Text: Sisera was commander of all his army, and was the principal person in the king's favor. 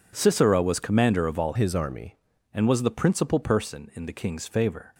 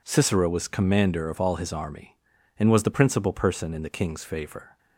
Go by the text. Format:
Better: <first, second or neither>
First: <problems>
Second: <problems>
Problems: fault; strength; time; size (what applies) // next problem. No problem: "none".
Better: second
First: changes voice from "his" to "army"; from 1.5 to 2.1 s; 0.6 s long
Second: none